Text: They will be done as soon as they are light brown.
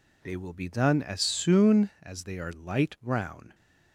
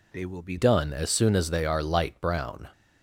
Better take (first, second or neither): first